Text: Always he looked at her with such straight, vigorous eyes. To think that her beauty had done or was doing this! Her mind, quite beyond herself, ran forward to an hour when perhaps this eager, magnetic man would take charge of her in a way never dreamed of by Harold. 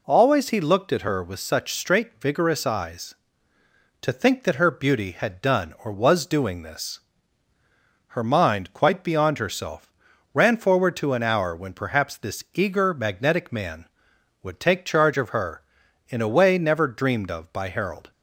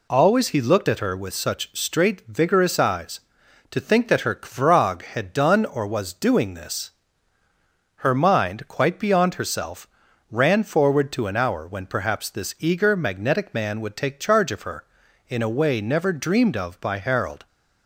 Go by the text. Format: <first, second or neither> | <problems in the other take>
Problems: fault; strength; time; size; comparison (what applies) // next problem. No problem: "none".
first | says "kvrog" for "beauty"; at 4.3 s